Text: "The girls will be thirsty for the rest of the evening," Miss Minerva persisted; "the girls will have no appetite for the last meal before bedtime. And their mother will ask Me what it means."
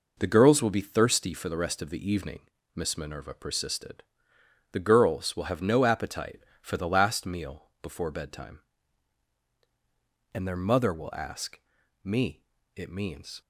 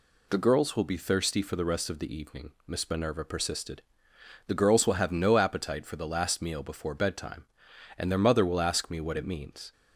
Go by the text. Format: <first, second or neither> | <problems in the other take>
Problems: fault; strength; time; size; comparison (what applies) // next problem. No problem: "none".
second | pauses between "ask" and "Me"; at 11.5 s; 0.44 s long // skips "what"; at 12.5 s